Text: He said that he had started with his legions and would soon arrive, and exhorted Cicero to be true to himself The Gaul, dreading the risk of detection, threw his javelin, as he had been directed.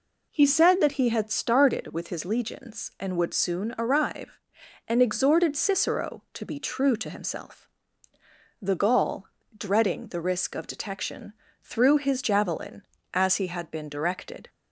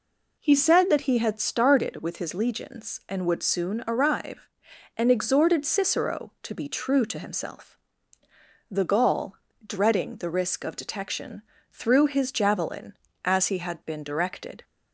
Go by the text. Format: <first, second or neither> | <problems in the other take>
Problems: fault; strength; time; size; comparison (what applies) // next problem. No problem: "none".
neither | pauses between "himself" and "The"; noticeable; the same in both